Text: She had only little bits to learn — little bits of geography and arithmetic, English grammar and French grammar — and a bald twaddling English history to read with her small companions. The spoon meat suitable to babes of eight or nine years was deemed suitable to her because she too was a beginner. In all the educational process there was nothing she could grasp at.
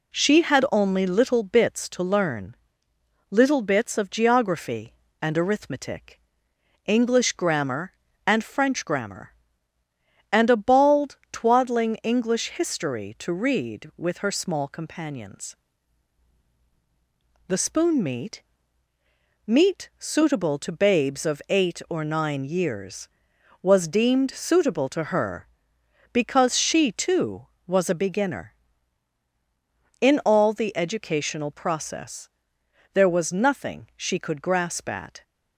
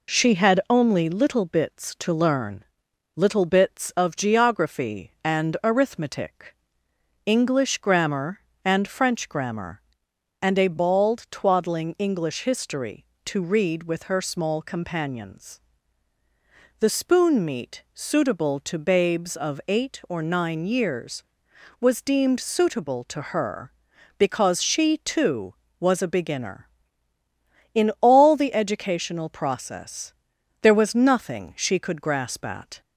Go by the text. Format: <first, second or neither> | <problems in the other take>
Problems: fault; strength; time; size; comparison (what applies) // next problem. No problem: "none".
second | says "meat" twice; at 19.4 s // pauses between "process" and "there"; noticeable; at 32.2 s; 0.64 s long; noticeable in the second